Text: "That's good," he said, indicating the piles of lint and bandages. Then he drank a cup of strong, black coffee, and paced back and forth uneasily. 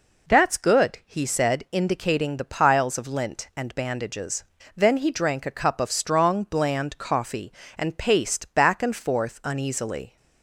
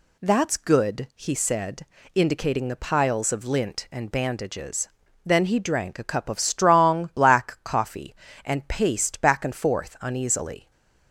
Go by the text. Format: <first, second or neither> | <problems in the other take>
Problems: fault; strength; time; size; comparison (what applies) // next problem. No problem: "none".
second | says "bland" for "black"; at 6.4 s